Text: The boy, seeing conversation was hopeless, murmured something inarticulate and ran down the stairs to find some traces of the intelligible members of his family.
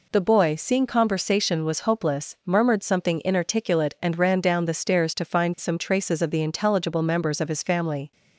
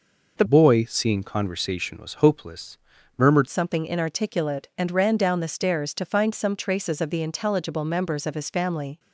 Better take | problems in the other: first | changes voice from "boy" to "murmured"; from 0.4 to 3.4 s; 3.0 s long

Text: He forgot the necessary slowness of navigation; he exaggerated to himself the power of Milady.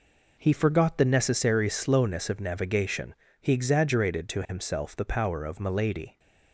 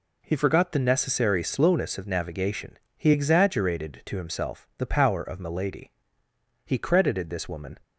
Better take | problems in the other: first | goes on to say "He credited this woman"; noticeable; from 6.6 s on; 1.1 s long

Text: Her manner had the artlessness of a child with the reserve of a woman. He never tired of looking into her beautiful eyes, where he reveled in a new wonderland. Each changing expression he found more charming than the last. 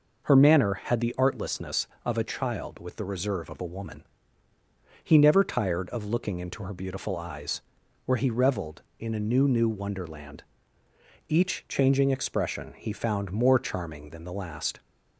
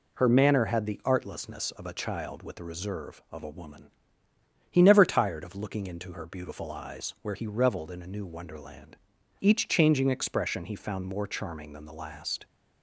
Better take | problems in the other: second | says "new" twice; at 9.4 s

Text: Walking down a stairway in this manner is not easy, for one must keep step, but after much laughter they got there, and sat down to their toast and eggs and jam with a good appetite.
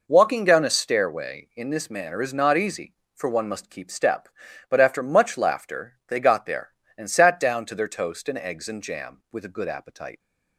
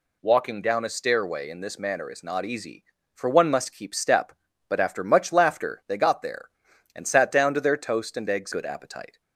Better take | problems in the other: first | skips "and jam with a"; at 8.5 s

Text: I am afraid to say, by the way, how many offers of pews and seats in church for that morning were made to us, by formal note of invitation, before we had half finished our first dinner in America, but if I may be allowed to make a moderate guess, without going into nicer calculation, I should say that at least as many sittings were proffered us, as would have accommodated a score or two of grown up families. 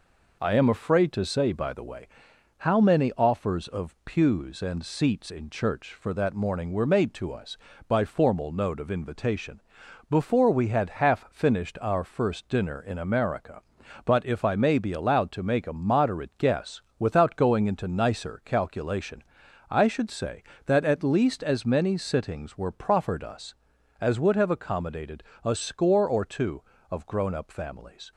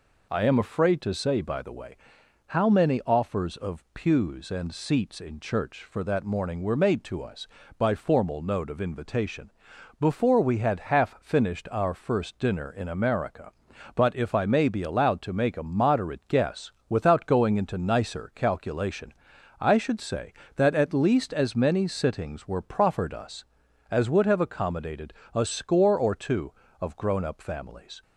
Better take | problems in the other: second | gets quieter; slight; throughout; 3 dB // pauses between "accommodated" and "a"; slight; at 25.2 s; 0.22 s long; slight in the second

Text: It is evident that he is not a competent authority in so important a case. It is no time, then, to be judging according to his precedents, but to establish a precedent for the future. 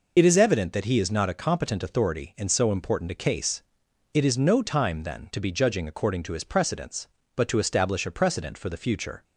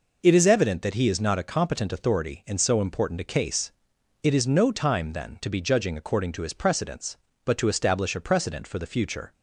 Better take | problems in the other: second | loses the start of "It"; at 0.1 s; 35 ms

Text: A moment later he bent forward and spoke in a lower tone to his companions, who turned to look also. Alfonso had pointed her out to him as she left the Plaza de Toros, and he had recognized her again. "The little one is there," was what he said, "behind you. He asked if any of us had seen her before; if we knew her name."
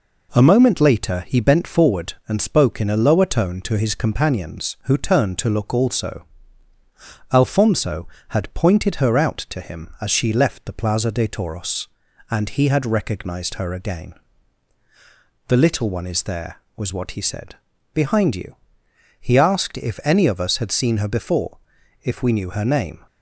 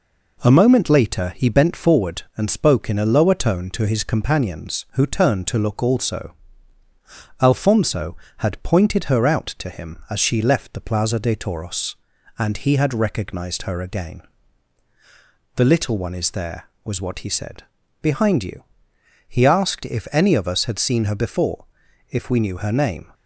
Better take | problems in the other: neither | none

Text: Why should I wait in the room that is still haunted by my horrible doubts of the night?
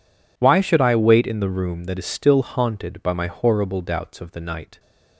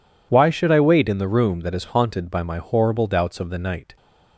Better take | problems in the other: first | skips "still"; at 1.8 s

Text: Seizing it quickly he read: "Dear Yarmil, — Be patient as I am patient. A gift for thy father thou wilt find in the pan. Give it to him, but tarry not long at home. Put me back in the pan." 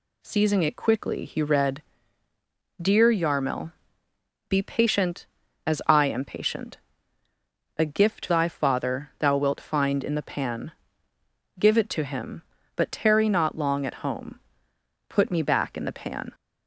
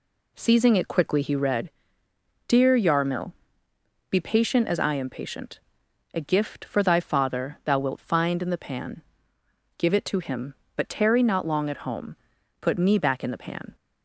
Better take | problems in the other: second | skips "for"; at 8.2 s

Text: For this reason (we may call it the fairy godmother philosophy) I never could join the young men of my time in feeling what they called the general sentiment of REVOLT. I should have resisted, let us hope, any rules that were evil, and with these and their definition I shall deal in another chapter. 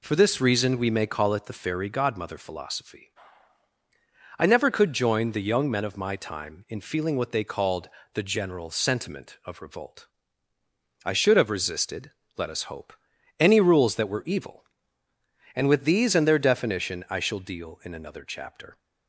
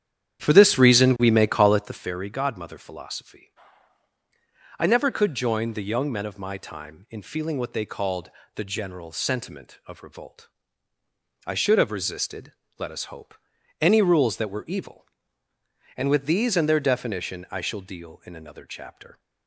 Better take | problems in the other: first | starts louder than the rest; strong; until 2.1 s; 10 dB // pauses between "called" and "the"; slight; at 8.2 s; 0.26 s long; slight in the first

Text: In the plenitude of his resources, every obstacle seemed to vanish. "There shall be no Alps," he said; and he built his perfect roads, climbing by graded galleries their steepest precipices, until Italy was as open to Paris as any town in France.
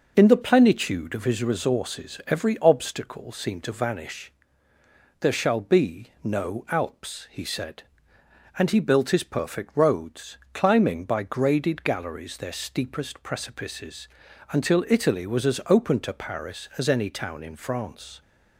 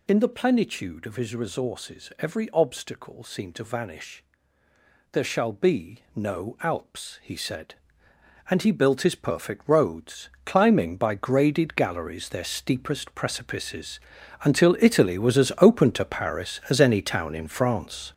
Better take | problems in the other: first | gets louder; strong; throughout; 8 dB

